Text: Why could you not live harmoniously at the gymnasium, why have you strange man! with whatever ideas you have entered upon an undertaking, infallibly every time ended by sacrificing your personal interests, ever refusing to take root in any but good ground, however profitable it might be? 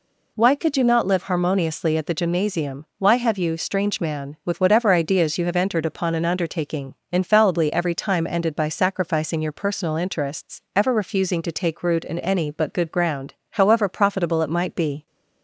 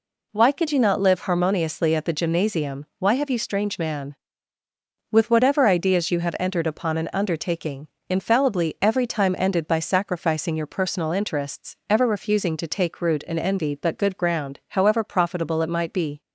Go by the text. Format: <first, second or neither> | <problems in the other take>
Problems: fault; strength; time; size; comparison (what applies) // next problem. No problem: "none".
first | says "envy" for "any"; at 13.3 s